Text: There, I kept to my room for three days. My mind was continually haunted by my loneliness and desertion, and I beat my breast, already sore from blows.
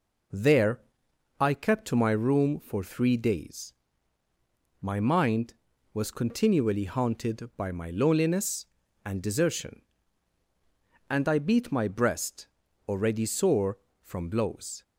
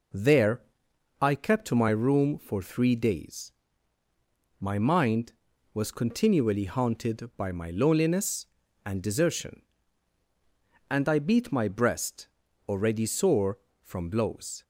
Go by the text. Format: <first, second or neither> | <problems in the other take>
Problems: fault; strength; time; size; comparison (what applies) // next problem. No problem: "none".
neither | none